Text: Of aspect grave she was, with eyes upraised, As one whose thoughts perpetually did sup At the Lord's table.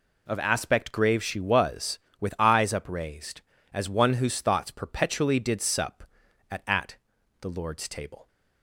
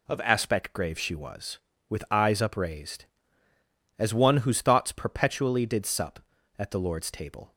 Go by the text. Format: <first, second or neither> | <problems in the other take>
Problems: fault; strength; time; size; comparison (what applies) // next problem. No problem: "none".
second | says "At" twice; at 6.6 s